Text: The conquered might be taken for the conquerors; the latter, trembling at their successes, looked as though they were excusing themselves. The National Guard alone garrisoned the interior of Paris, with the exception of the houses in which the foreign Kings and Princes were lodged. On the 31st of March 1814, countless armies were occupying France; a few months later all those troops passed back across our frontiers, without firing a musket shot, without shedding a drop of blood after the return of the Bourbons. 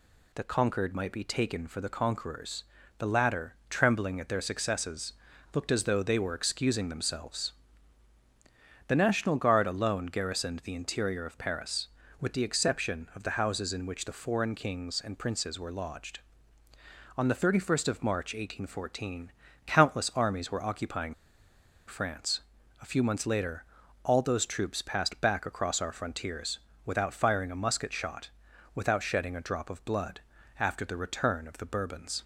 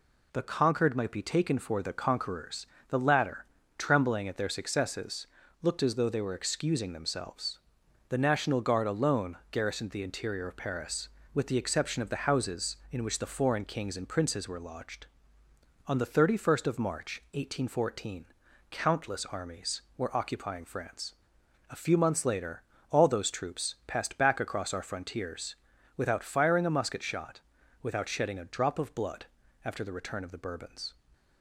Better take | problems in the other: second | pauses between "occupying" and "France"; noticeable; at 21.1 s; 0.72 s long // pauses between "later" and "all"; at 23.6 s; 0.40 s long; slight in the second // pauses between "blood" and "after"; slight; at 30.2 s; 0.36 s long; also in the second

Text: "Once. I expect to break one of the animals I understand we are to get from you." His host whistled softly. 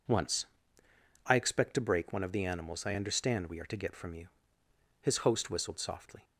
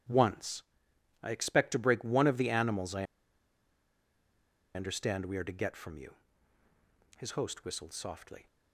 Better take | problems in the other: first | starts louder than the rest; strong; until 1.6 s; 11 dB // pauses between "I" and "understand"; strong; at 3.0 s; 1.7 s long

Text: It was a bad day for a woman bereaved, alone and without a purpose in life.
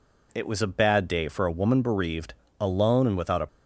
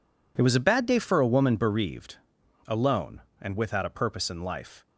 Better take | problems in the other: second | stops before "purpose in life"; at 3.4 s

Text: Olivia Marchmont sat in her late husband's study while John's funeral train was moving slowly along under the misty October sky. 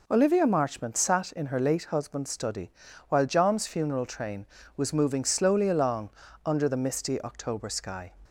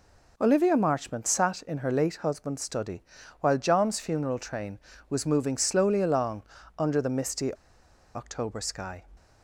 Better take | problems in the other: first | pauses between "study" and "while"; at 3.0 s; 0.38 s long; also in the first // pauses between "along" and "under"; slight; at 6.4 s; 0.36 s long; slight in the first // pauses between "misty" and "October"; noticeable; at 7.5 s; 0.61 s long

